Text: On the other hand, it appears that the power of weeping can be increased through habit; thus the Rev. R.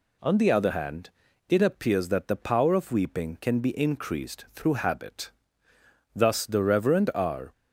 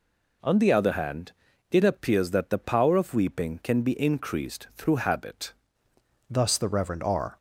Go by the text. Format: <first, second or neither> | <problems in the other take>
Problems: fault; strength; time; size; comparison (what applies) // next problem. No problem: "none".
first | changes voice at "thus"; from 6.3 s on; 1.0 s long